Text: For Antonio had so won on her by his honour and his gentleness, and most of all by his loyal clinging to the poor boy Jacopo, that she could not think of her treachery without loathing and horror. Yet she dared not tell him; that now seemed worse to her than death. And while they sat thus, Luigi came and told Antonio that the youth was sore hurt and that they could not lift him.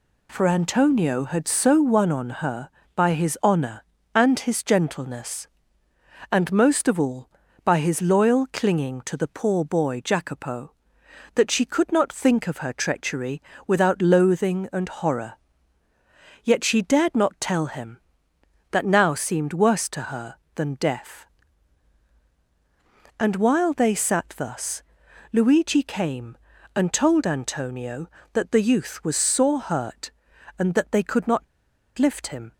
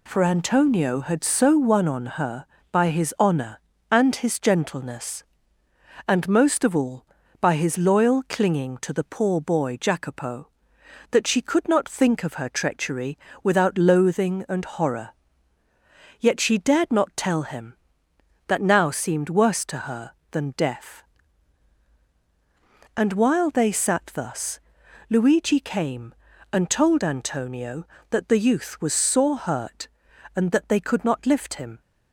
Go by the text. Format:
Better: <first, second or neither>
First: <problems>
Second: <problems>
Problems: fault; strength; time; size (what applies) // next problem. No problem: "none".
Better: second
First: pauses between "treachery" and "without"; slight; at 13.4 s; 0.24 s long // pauses between "not" and "lift"; noticeable; at 31.4 s; 0.53 s long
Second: pauses between "treachery" and "without"; slight; at 13.1 s; 0.24 s long